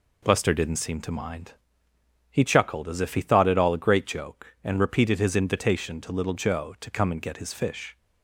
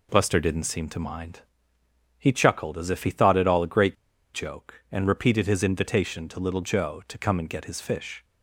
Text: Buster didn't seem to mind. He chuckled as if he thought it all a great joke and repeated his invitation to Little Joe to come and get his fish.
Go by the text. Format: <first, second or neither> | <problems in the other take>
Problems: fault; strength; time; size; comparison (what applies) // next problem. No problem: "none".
first | pauses between "great" and "joke"; at 3.9 s; 0.38 s long